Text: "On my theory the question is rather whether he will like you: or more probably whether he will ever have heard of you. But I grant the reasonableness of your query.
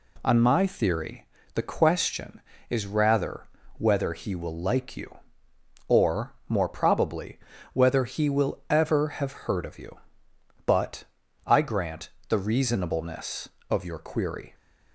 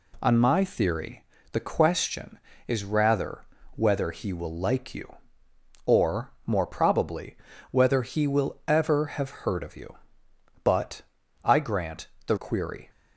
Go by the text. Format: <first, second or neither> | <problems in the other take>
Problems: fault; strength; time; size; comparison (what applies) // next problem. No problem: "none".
first | pauses between "theory" and "the"; slight; at 1.2 s; 0.26 s long; slight in the first // pauses between "rather" and "whether"; slight; at 3.4 s; 0.30 s long; slight in the first // pauses between "or" and "more"; slight; at 6.3 s; 0.16 s long; slight in the first // pauses between "probably" and "whether"; slight; at 7.3 s; 0.36 s long; slight in the first // pauses between "But" and "I"; at 11.0 s; 0.40 s long; also in the first // pauses between "grant" and "the"; slight; at 12.0 s; 0.20 s long; slight in the first // skips "reasonableness of your"; at 12.3 s